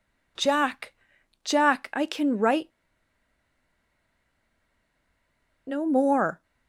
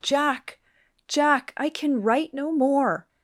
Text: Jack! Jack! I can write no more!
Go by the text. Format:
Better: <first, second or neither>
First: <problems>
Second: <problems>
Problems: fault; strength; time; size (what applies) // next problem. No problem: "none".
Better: second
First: pauses between "write" and "no"; strong; at 2.7 s; 2.9 s long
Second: none